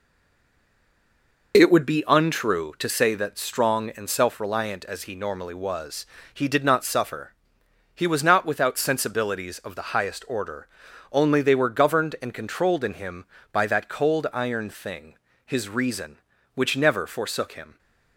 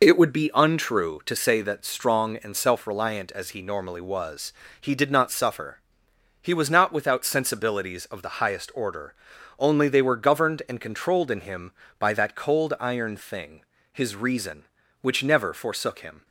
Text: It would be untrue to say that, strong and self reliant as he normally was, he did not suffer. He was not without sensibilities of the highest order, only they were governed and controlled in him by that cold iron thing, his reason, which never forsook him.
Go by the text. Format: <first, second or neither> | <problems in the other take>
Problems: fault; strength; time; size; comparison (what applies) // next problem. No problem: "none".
second | stays silent before the first word; noticeable; until 1.5 s; 1.5 s long